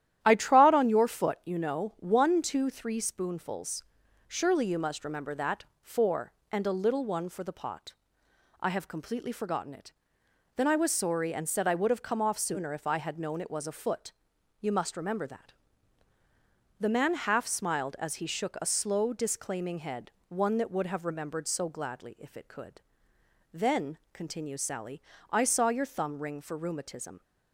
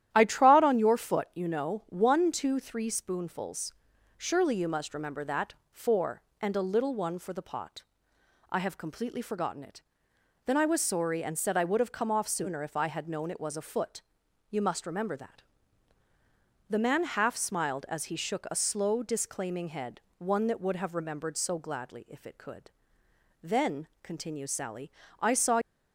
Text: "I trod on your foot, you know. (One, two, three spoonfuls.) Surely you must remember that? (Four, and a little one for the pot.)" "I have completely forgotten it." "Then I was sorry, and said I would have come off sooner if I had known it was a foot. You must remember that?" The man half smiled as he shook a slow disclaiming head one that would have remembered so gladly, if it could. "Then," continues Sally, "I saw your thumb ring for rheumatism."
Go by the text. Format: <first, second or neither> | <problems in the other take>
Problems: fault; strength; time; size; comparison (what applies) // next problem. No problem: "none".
first | starts louder than the rest; strong; until 1.1 s; 11.5 dB; strong in the first // pauses between "head" and "one"; slight; at 20.0 s; 0.18 s long; slight in the first // stops before "your thumb ring for rheumatism"; at 25.6 s